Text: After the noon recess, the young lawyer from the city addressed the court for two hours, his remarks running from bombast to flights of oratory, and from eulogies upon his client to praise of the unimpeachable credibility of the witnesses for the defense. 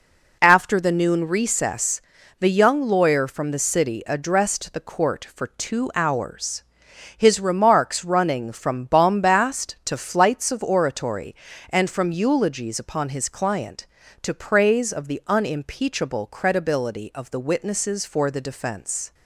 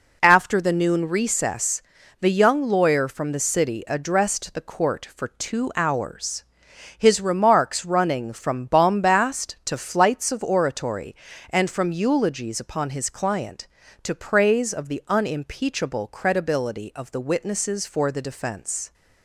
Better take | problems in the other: neither | none

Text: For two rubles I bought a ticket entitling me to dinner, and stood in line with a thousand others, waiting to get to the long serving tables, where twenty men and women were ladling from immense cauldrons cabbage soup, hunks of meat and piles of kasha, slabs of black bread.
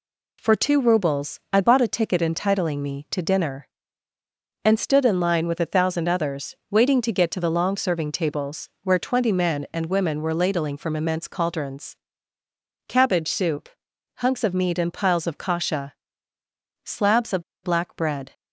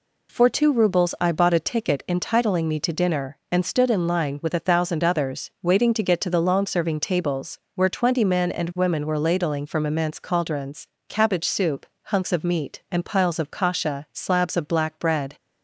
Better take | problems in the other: second | pauses between "cauldrons" and "cabbage"; noticeable; at 11.9 s; 0.90 s long; slight in the second // pauses between "of" and "black"; slight; at 17.4 s; 0.19 s long

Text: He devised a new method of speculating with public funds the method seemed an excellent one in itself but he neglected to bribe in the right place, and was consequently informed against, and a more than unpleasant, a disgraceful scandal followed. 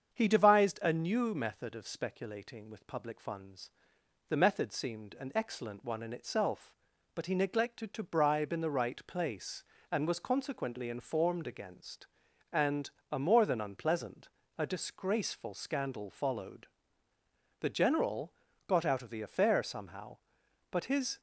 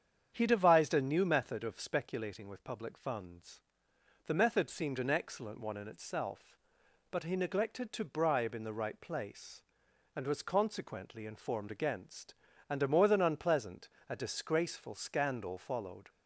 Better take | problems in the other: second | starts louder than the rest; strong; until 1.1 s; 7.5 dB; strong in the second // pauses between "funds" and "the"; noticeable; at 3.6 s; 0.58 s long; noticeable in the second // pauses between "and" and "a"; slight; at 12.8 s; 0.22 s long // goes on to say "The general got out of the affair somehow but his"; strong; from 17.5 s on; 3.6 s long

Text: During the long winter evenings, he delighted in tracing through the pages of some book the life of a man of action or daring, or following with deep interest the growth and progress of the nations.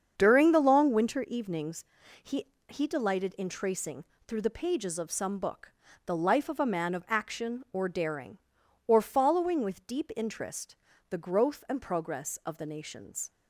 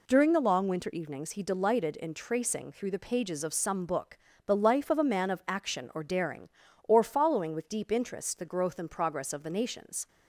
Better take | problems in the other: second | starts louder than the rest; strong; until 1.1 s; 7.5 dB // says "he" twice; at 2.6 s // pauses between "tracing" and "through"; slight; at 4.0 s; 0.22 s long // pauses between "book" and "the"; slight; at 5.7 s; 0.34 s long; slight in the second // pauses between "interest" and "the"; slight; at 10.7 s; 0.36 s long

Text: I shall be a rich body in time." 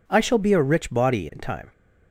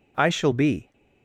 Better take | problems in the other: first | stops before "a rich body in time"; at 0.9 s

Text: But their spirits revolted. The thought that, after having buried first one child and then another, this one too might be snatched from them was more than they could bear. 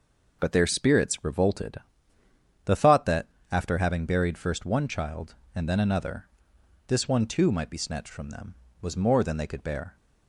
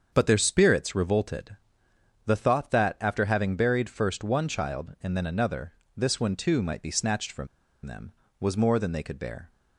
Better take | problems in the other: first | starts louder than the rest; until 1.1 s; 7 dB // pauses between "from" and "them"; at 7.4 s; 0.38 s long

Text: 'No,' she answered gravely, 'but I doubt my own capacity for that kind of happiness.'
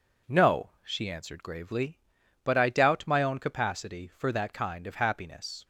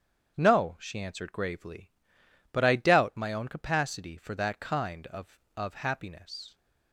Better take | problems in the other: first | starts louder than the rest; strong; until 1.3 s; 8 dB // says "of" twice; at 5.5 s

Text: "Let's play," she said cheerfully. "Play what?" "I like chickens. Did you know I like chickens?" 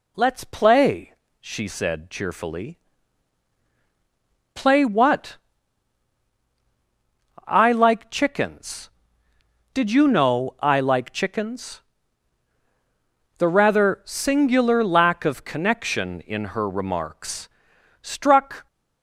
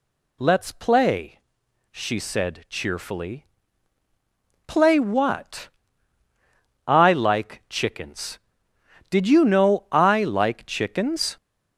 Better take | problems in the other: second | goes on to say "The rather singular lack of connection in her remarks struck"; strong; from 13.3 s on; 5.2 s long

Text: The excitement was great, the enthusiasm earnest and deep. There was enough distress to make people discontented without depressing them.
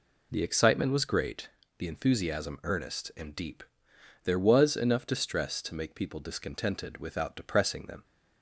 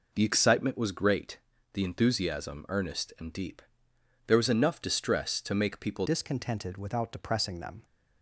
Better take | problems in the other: first | changes voice at "discontented"; from 6.0 s on; 1.8 s long

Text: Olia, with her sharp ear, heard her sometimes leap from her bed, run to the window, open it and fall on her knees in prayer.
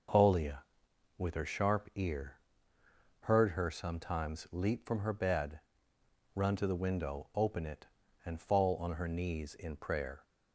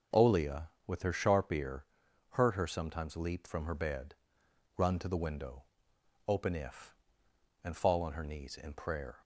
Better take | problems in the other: first | says "if" for "it"; at 6.5 s

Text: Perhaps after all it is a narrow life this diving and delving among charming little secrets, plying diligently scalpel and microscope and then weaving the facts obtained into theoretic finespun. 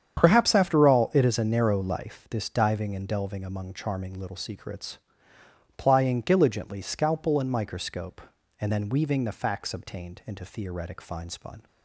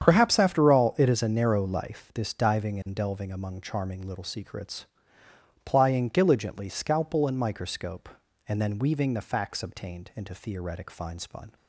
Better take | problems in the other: neither | starts louder than the rest; strong; the same in both

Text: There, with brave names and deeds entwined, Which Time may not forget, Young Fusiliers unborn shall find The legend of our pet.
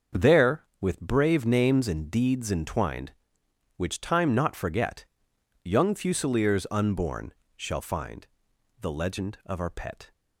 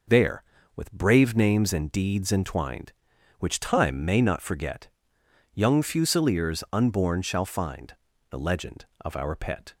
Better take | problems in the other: second | starts louder than the rest; until 1.3 s; 6.5 dB // skips "may"; at 4.3 s // pauses between "unborn" and "shall"; slight; at 7.3 s; 0.24 s long // pauses between "find" and "The"; noticeable; at 8.2 s; 0.52 s long; also in the second

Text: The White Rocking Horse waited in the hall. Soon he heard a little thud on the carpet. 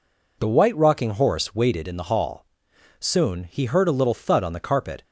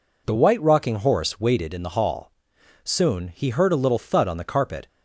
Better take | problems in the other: neither | none

